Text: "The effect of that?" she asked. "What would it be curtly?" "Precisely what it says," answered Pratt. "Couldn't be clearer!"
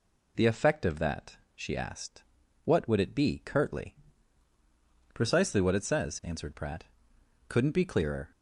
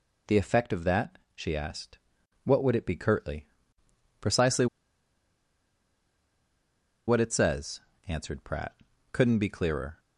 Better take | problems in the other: first | pauses between "Precisely" and "what"; strong; at 4.6 s; 2.4 s long

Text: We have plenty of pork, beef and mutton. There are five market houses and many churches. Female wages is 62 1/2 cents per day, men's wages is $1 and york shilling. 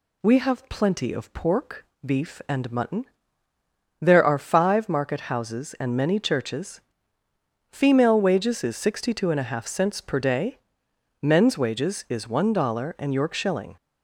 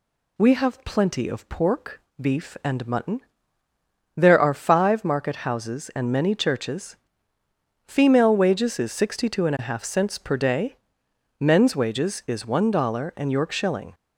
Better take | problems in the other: neither | none

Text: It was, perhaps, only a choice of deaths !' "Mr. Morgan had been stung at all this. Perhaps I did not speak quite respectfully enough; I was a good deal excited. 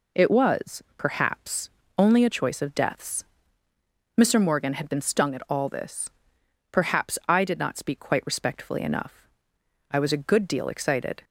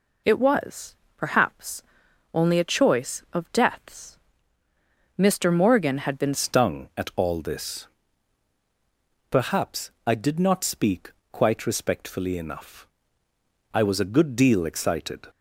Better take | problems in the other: first | changes voice at "stung"; from 6.3 s on; 8.9 s long // pauses between "speak" and "quite"; slight; at 11.1 s; 0.20 s long

